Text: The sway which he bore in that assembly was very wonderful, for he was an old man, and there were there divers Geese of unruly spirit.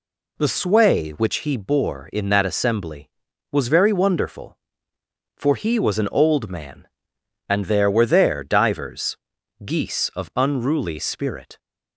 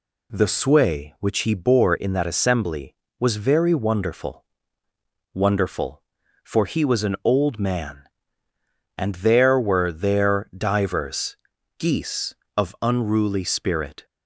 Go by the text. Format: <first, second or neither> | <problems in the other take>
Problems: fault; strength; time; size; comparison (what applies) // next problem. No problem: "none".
first | says "wonderful" twice; at 5.3 s // pauses between "divers" and "Geese"; at 11.3 s; 0.44 s long; noticeable in the first